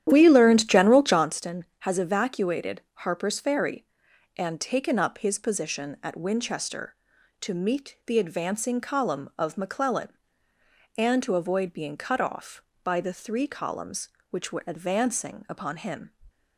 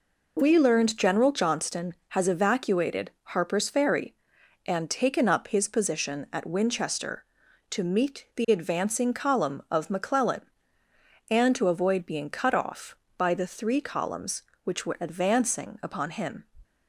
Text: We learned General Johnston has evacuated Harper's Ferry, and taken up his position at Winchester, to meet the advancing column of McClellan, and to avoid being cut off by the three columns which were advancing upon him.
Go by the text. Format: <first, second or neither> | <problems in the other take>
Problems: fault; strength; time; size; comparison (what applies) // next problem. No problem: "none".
second | starts louder than the rest; strong; until 1.3 s; 11 dB